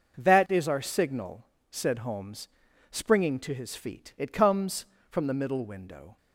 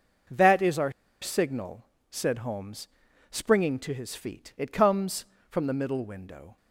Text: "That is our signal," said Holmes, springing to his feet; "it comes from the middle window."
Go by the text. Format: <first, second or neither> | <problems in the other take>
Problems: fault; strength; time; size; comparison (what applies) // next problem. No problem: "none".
first | pauses between "our" and "signal"; slight; at 0.9 s; 0.30 s long